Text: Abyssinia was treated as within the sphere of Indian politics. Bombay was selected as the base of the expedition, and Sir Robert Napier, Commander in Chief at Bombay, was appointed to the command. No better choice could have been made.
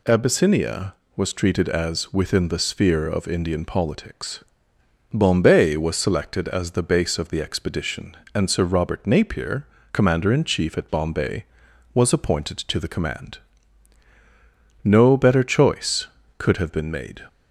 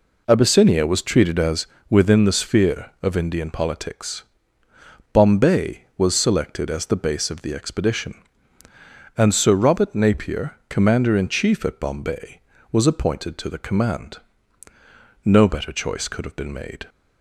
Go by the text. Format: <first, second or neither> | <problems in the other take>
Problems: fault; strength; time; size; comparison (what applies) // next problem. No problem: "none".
first | starts louder than the rest; until 1.7 s; 4 dB // pauses between "as" and "within"; slight; at 1.6 s; 0.24 s long